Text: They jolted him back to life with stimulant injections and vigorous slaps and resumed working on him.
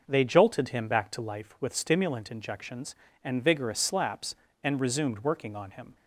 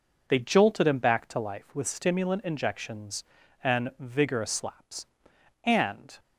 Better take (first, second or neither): first